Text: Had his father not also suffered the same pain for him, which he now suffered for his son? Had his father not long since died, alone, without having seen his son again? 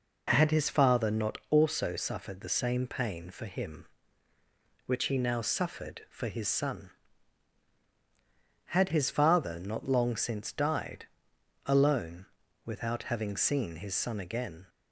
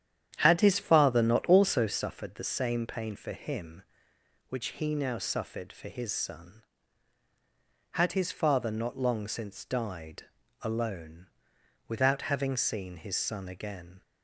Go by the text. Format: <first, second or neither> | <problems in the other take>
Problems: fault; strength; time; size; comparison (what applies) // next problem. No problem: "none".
first | starts louder than the rest; strong; until 2.0 s; 9.5 dB